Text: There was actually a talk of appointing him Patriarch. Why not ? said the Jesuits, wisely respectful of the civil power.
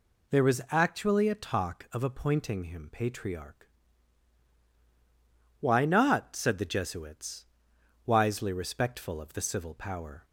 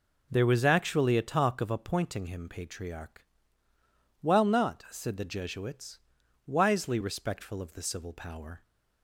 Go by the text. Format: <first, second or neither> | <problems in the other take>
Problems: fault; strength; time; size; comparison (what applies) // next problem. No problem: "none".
first | says "While" for "Why"; at 4.2 s